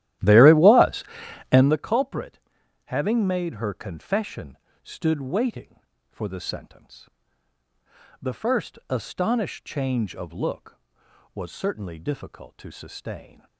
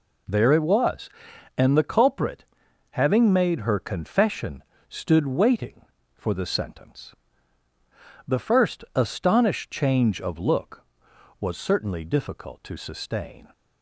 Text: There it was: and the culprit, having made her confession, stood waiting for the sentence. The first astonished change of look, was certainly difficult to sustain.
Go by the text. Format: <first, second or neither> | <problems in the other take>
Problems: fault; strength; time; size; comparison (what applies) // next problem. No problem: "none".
second | starts louder than the rest; strong; until 1.8 s; 13.5 dB